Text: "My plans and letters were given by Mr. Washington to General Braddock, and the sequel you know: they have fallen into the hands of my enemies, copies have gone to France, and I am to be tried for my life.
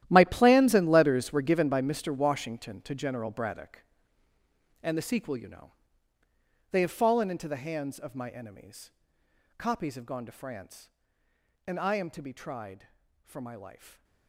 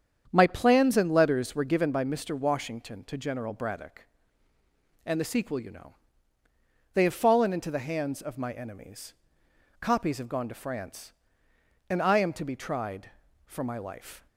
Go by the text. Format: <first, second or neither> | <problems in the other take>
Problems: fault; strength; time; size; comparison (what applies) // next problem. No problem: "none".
second | gets quieter; strong; throughout; 16.5 dB // starts louder than the rest; strong; until 1.1 s; 12.5 dB; strong in the second